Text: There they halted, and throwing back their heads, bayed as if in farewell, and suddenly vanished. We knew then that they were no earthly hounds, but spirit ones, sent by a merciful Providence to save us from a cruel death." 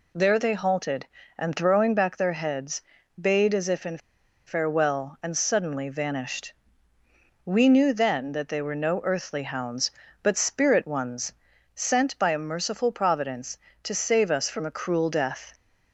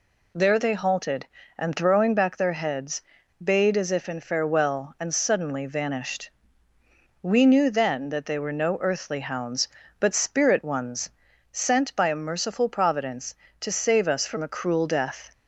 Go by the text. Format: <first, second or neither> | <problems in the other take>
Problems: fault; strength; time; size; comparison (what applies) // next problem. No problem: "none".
second | pauses between "in" and "farewell"; noticeable; at 3.9 s; 0.47 s long